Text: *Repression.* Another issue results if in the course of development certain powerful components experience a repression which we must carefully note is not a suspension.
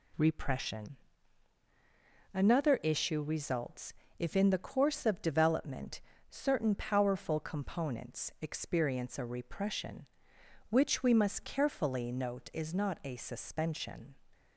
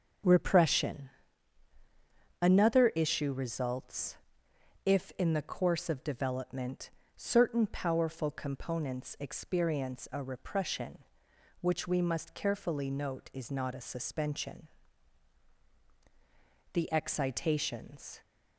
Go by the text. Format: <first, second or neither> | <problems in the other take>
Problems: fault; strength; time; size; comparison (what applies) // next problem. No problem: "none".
first | starts louder than the rest; until 2.5 s; 6.5 dB // pauses between "results" and "if"; noticeable; at 4.1 s; 0.70 s long; slight in the first // pauses between "development" and "certain"; slight; at 6.8 s; 0.26 s long; slight in the first // goes on to say "The excitations"; from 16.7 s on; 1.4 s long